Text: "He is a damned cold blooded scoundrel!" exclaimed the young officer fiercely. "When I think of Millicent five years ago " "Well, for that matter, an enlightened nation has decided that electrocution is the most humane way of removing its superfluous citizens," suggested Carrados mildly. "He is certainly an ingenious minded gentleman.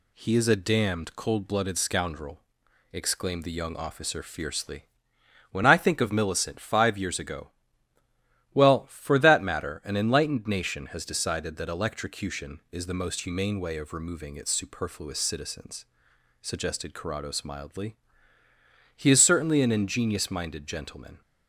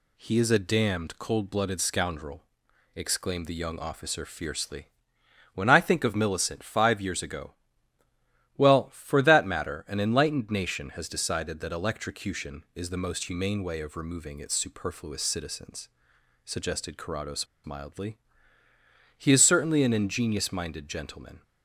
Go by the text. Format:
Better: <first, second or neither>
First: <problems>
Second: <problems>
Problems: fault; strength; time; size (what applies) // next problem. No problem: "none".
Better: first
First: none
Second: pauses between "Carrados" and "mildly"; slight; at 17.4 s; 0.18 s long